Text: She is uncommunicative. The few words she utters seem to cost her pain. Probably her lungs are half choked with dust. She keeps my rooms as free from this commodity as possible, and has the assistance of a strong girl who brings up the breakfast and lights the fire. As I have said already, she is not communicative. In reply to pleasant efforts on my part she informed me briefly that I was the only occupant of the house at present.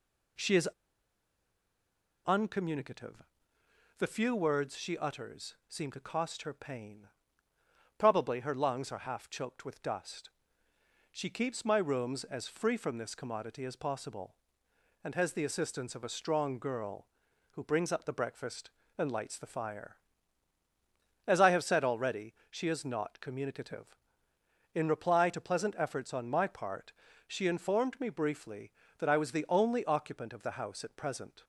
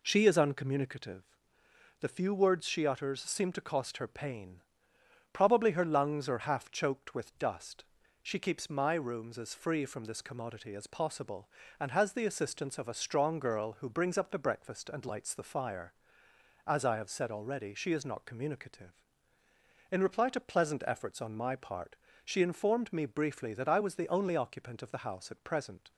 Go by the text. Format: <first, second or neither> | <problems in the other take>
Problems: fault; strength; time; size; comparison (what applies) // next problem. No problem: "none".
second | pauses between "is" and "uncommunicative"; strong; at 0.6 s; 1.5 s long // pauses between "part" and "she"; slight; at 26.9 s; 0.34 s long; slight in the second